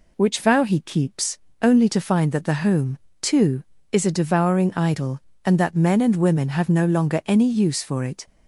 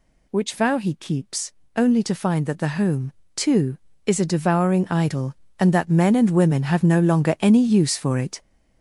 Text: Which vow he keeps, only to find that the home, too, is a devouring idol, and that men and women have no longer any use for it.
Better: first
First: none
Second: gets louder; strong; throughout; 9 dB

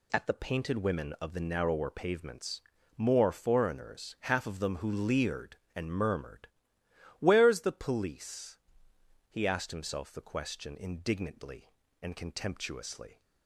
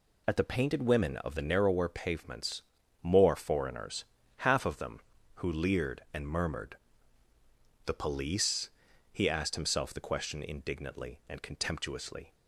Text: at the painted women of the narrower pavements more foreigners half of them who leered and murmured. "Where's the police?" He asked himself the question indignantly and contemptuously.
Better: first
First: pauses between "pavements" and "more"; slight; at 2.6 s; 0.36 s long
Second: pauses between "pavements" and "more"; at 2.6 s; 0.40 s long // pauses between "foreigners" and "half"; slight; at 4.0 s; 0.34 s long // skips "Where's"; at 7.3 s

